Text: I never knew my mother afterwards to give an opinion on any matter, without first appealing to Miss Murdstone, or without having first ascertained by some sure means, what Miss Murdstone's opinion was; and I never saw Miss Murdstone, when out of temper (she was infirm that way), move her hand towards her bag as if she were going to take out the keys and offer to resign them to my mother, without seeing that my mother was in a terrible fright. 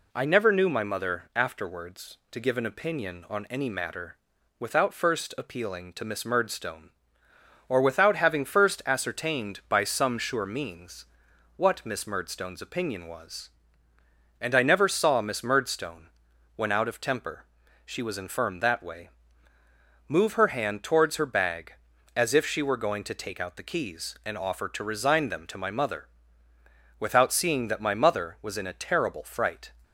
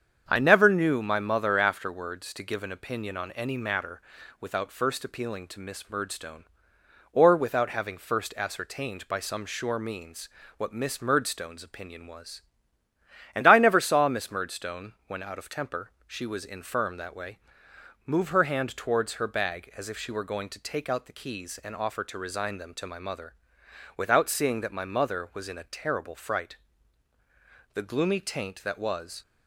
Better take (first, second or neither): first